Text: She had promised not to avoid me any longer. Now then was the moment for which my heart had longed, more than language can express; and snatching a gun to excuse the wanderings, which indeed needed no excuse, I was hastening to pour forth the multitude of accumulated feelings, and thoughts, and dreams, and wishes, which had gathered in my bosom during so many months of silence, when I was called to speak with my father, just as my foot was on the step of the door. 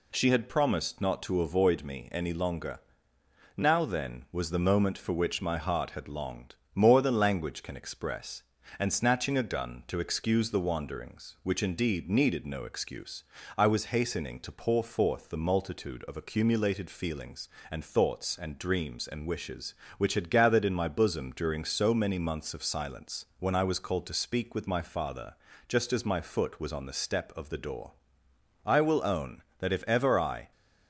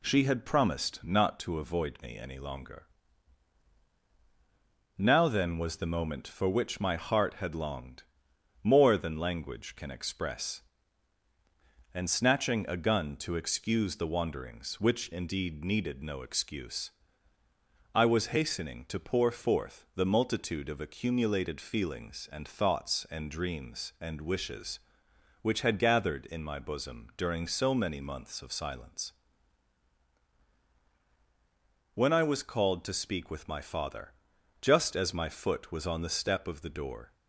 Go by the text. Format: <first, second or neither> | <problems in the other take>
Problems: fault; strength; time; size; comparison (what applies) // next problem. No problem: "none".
second | goes on to say "I will own that if ever I"; strong; from 28.6 s on; 1.8 s long